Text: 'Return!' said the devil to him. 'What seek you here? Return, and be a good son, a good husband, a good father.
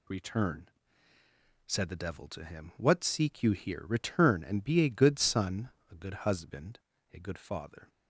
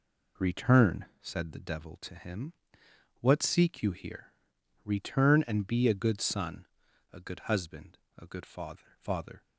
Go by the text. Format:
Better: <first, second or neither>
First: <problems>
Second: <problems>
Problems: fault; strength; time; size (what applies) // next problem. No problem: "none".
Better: first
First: none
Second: says "father" twice; at 8.9 s